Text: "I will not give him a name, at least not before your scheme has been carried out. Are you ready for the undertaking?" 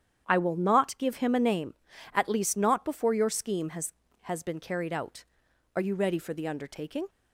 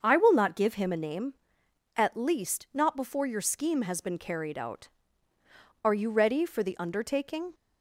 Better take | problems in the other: second | starts louder than the rest; strong; until 1.2 s; 9 dB; also in the second // says "has" twice; at 4.2 s

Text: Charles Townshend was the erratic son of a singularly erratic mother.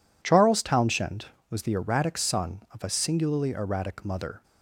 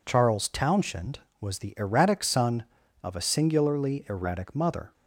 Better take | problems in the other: neither | none

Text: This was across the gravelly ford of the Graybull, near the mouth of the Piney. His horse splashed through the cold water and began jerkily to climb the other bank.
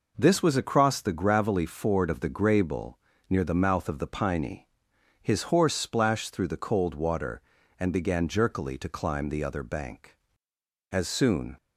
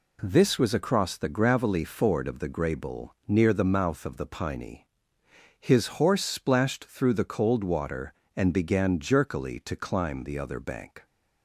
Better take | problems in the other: second | goes on to say "As soon"; noticeable; from 10.9 s on; 0.64 s long

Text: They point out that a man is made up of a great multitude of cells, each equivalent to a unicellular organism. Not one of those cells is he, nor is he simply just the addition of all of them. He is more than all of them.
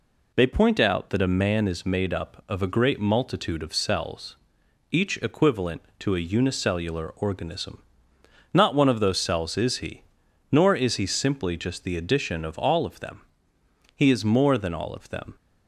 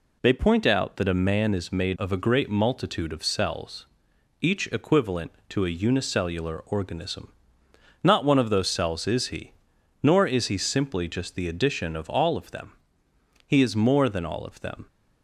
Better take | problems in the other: first | skips "up"; at 1.9 s

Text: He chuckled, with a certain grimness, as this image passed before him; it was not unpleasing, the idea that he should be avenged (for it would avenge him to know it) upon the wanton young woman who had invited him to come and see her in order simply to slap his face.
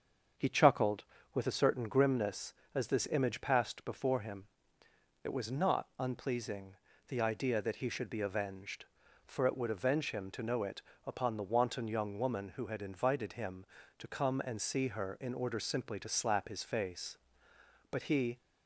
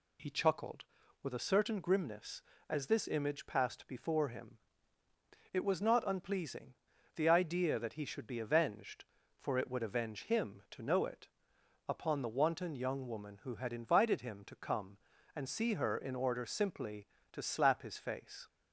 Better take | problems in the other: second | starts louder than the rest; until 1.6 s; 7 dB // goes on to say "But he"; slight; from 17.8 s on; 0.48 s long

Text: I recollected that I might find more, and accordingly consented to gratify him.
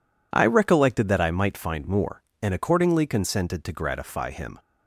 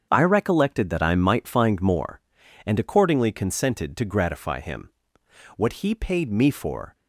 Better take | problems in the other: first | starts louder than the rest; strong; until 1.1 s; 7.5 dB // goes on to say "What he paid me for"; from 5.5 s on; 1.3 s long

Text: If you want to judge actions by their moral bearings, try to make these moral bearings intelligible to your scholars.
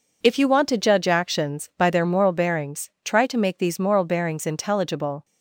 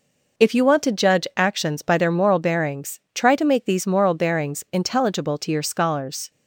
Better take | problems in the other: second | stops before "to your scholars"; at 5.2 s

